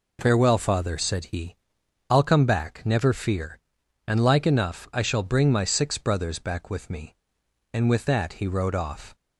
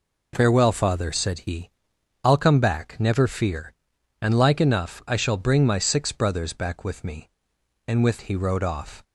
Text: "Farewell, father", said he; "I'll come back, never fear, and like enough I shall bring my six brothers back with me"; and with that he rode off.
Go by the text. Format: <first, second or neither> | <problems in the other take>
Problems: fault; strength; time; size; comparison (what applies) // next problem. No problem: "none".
first | skips "that"; at 8.2 s